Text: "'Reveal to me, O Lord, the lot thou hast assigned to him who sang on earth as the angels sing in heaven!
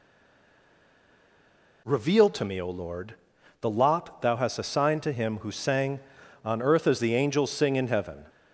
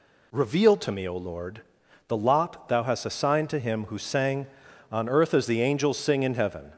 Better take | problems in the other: second | stays silent before the first word; noticeable; until 1.8 s; 1.8 s long

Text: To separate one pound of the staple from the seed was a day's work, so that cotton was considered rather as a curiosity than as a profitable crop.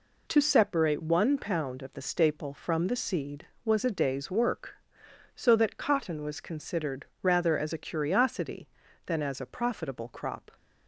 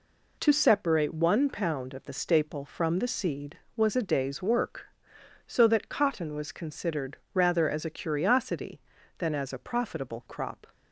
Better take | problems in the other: neither | pauses between "considered" and "rather"; slight; the same in both

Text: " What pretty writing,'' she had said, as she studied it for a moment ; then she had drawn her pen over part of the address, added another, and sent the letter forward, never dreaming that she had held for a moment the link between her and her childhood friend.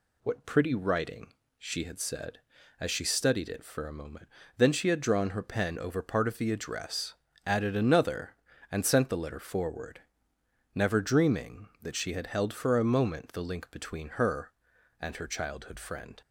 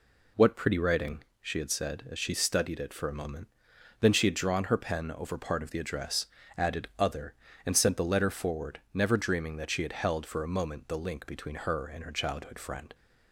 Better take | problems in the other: first | says "other" for "another"; at 6.9 s

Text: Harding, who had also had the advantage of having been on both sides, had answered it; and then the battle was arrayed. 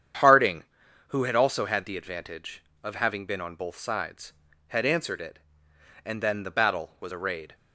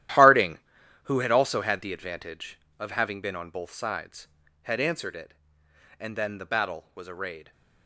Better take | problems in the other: first | gets quieter; strong; throughout; 13.5 dB // starts louder than the rest; strong; until 1.6 s; 12.5 dB; strong in the first

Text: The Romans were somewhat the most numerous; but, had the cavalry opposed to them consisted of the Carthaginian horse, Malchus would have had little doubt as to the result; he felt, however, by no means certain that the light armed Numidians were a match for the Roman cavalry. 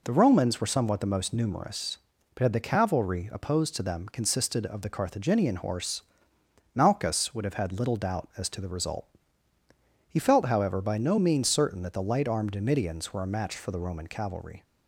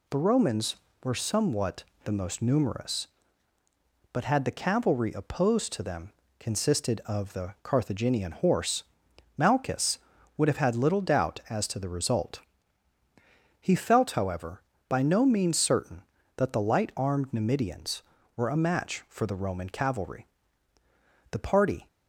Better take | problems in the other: first | pauses between "somewhat" and "the"; slight; at 1.8 s; 0.22 s long // pauses between "them" and "consisted"; slight; at 6.1 s; 0.26 s long // goes on to say "The party"; from 21.3 s on; 0.56 s long

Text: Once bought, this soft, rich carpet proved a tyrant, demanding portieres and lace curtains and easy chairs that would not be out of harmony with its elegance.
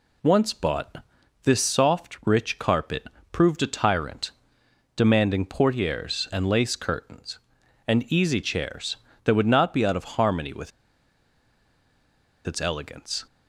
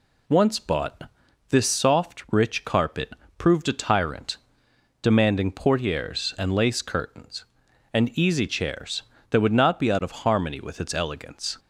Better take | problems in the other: second | pauses between "carpet" and "proved"; slight; at 3.0 s; 0.24 s long; slight in the second // pauses between "with" and "its"; strong; at 10.7 s; 1.7 s long

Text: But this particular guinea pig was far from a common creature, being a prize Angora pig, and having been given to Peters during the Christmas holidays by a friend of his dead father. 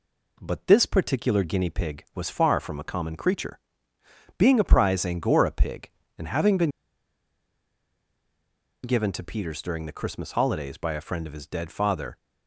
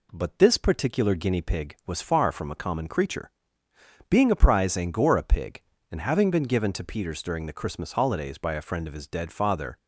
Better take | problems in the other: second | pauses between "been" and "given"; strong; at 6.6 s; 2.1 s long

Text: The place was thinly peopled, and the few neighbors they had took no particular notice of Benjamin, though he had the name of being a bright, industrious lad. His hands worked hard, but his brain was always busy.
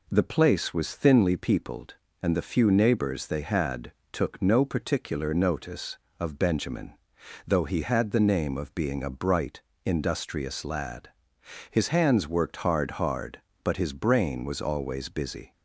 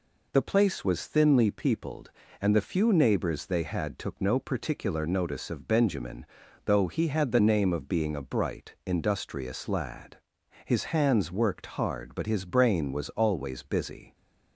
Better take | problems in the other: second | pauses between "had" and "took"; slight; at 3.9 s; 0.18 s long // says "hard" twice; at 12.9 s

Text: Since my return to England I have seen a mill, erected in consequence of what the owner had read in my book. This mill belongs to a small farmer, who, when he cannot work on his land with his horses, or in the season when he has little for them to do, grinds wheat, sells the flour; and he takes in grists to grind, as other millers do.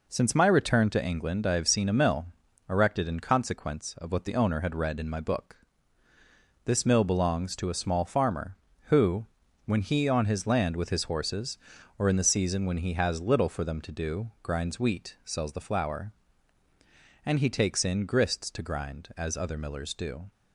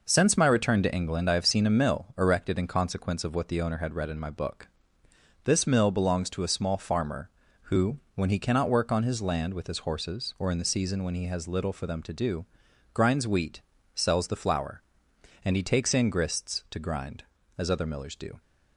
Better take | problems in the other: second | skips "cannot work"; at 10.0 s

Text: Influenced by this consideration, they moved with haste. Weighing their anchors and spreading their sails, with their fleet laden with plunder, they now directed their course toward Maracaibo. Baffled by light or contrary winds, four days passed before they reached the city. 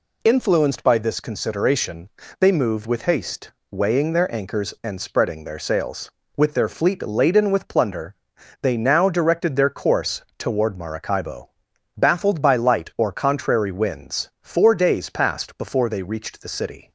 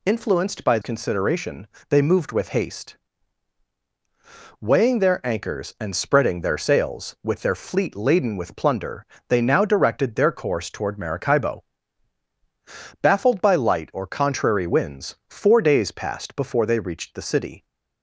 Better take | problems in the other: first | skips "this"; at 0.8 s

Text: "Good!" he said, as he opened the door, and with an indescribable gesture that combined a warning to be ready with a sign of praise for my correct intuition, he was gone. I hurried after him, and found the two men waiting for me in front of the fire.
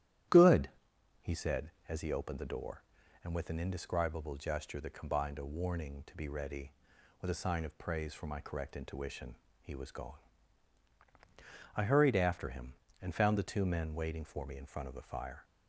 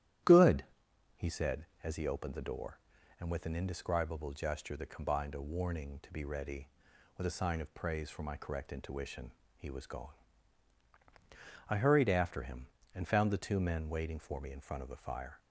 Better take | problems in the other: neither | starts louder than the rest; strong; the same in both

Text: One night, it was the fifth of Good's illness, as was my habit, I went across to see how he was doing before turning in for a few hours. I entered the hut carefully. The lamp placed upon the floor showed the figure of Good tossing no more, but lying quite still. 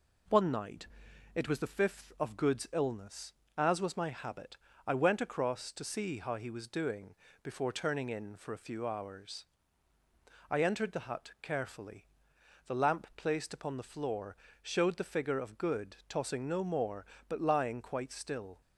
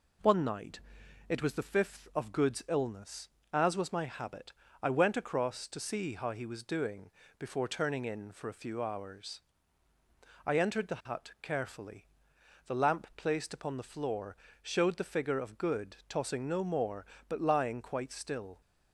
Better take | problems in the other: neither | pauses between "doing" and "before"; slight; the same in both // pauses between "floor" and "showed"; slight; the same in both

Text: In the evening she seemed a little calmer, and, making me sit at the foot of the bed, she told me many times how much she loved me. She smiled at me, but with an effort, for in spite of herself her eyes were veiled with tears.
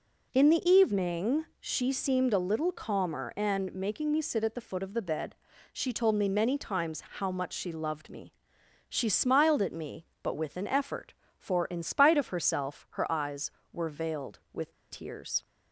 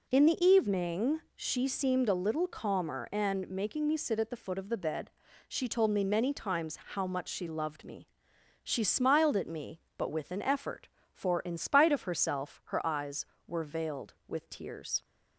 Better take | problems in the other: second | pauses between "times" and "how"; slight; at 7.0 s; 0.16 s long; slight in the second // pauses between "with" and "tears"; slight; at 14.7 s; 0.16 s long

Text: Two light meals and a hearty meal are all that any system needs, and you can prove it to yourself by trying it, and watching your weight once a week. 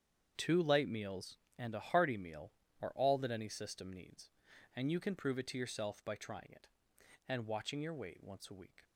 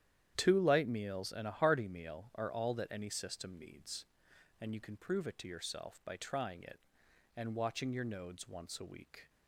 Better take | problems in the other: first | starts louder than the rest; strong; until 1.3 s; 10.5 dB; strong in the first // says "nodes" for "weight"; at 8.0 s

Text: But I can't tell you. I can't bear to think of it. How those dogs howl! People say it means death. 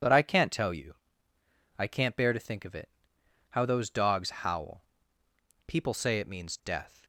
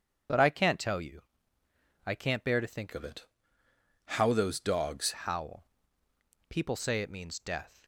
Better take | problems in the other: first | changes voice from "of" to "dogs"; from 2.9 to 5.1 s; 2.2 s long

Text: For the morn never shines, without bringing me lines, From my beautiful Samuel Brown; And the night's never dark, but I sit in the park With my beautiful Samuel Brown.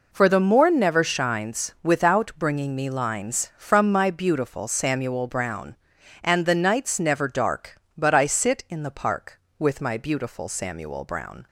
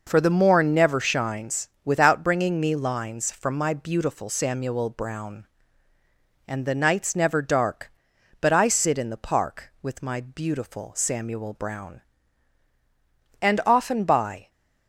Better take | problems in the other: first | goes on to say "And often by"; noticeable; from 13.4 s on; 1.0 s long

